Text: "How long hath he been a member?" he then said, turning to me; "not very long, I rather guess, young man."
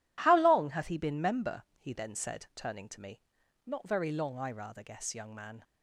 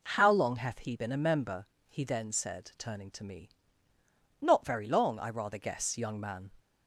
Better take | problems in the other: second | skips "a"; at 1.2 s

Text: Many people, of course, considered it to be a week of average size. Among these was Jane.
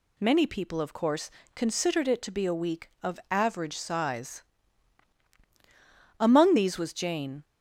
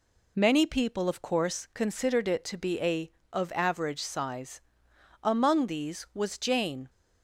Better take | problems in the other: first | skips "week"; at 3.2 s

